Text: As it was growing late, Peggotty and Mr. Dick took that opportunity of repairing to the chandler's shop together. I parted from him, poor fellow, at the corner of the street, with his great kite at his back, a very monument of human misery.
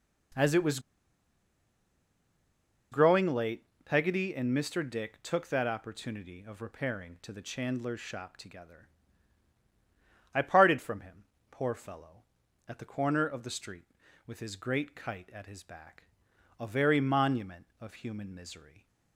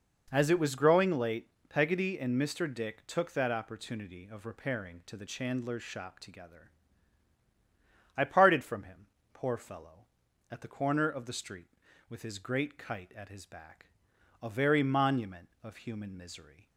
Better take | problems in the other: second | pauses between "was" and "growing"; strong; at 0.7 s; 2.1 s long

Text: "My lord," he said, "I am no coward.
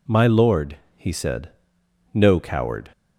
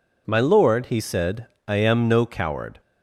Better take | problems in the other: second | skips "I am"; at 1.8 s

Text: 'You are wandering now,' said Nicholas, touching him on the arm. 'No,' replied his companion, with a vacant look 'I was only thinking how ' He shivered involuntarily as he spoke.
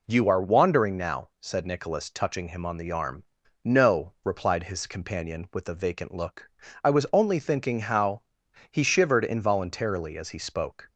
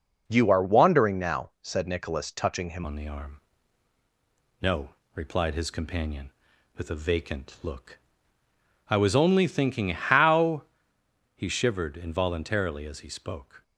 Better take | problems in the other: first | changes voice at "on"; from 2.8 s on; 10.8 s long // pauses between "look" and "I"; noticeable; at 8.0 s; 0.90 s long; slight in the first

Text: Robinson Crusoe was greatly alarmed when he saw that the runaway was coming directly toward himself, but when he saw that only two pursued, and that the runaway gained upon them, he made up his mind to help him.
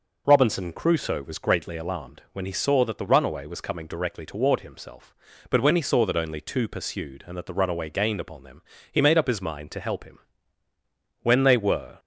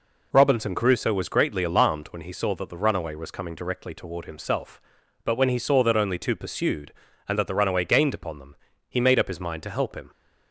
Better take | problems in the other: second | goes on to say "When they were"; noticeable; from 11.2 s on; 0.78 s long

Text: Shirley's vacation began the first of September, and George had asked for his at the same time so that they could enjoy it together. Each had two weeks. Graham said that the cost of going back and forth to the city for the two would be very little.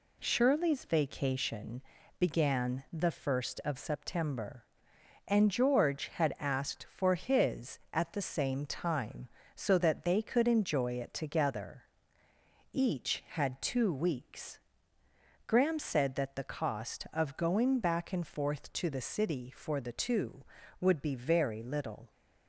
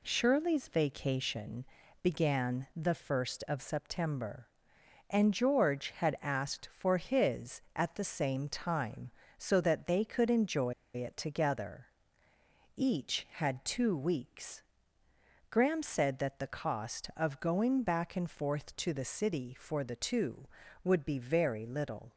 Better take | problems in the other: first | pauses between "vacation" and "began"; at 1.6 s; 0.40 s long; also in the first // pauses between "enjoy" and "it"; slight; at 10.7 s; 0.22 s long

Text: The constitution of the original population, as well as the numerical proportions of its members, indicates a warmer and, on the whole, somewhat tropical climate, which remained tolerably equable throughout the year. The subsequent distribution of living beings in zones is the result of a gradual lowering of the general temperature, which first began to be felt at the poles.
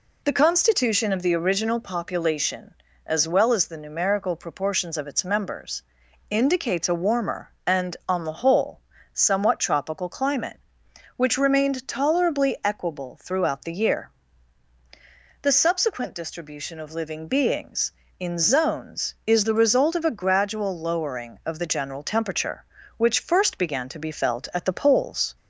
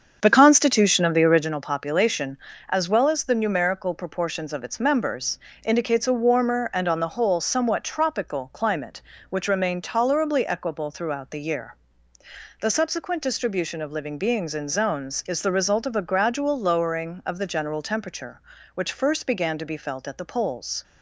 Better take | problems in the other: first | starts louder than the rest; strong; until 1.5 s; 7.5 dB

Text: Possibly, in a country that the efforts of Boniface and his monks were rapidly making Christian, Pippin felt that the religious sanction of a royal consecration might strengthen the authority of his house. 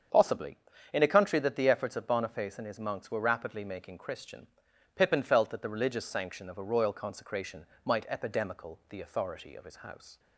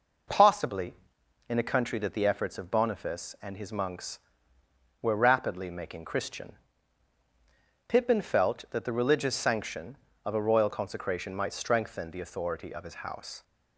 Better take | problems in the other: second | starts louder than the rest; strong; until 1.4 s; 7.5 dB // pauses between "consecration" and "might"; slight; at 7.6 s; 0.20 s long // says "epidemical" for "strengthen"; at 8.0 s

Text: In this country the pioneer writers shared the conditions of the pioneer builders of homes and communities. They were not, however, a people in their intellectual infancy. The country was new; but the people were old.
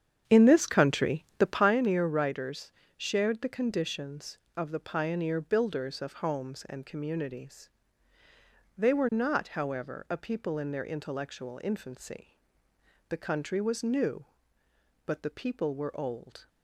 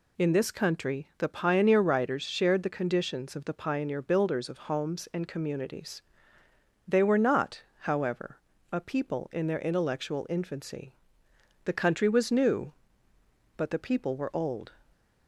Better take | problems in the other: second | starts louder than the rest; strong; until 1.8 s; 8.5 dB // pauses between "writers" and "shared"; slight; at 2.7 s; 0.26 s long

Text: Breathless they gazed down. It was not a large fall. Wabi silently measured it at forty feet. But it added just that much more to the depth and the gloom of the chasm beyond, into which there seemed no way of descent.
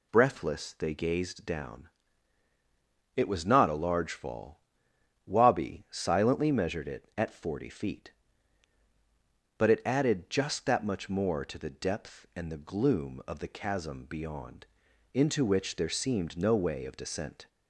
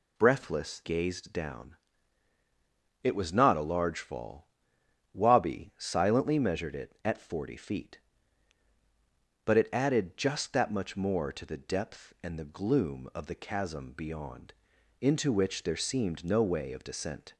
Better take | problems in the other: first | skips "they"; at 0.8 s

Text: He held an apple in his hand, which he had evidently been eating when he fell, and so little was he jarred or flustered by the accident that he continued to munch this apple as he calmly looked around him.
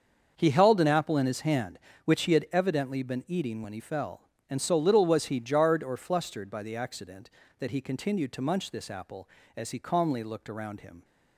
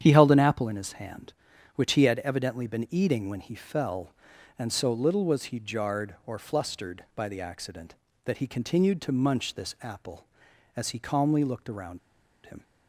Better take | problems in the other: first | starts louder than the rest; strong; until 1.0 s; 9 dB; also in the first // pauses between "around" and "him"; noticeable; at 11.9 s; 0.47 s long

